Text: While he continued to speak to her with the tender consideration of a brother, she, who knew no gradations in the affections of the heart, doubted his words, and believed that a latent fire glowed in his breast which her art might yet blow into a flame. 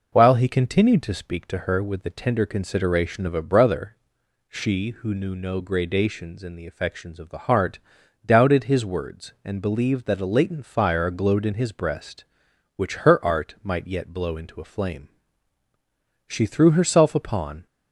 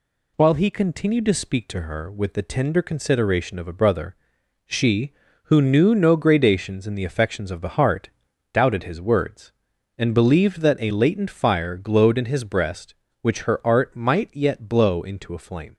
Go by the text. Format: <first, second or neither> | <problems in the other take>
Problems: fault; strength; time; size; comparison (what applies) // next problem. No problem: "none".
second | goes on to say "She threw herself upon"; from 16.2 s on; 1.3 s long